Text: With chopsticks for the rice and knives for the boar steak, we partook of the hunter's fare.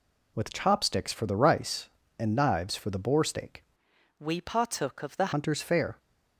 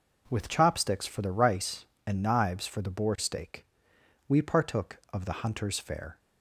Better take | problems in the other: second | changes voice from "we" to "the"; from 4.1 to 5.3 s; 1.2 s long

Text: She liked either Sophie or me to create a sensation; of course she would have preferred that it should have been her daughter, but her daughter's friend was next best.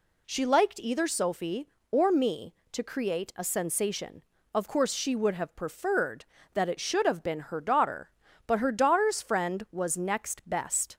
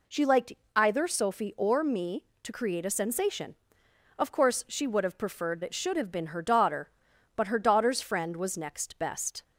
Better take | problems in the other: first | pauses between "liked" and "either"; slight; at 0.5 s; 0.22 s long // skips "that"; at 5.6 s

